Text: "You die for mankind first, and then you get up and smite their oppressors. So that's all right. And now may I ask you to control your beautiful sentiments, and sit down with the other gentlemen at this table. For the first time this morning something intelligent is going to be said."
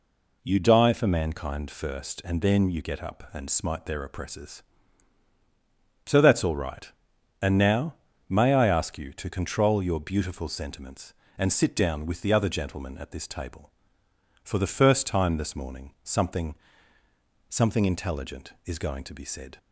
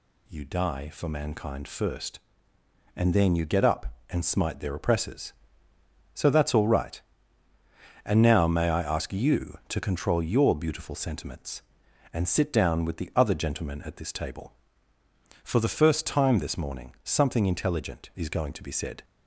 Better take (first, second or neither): second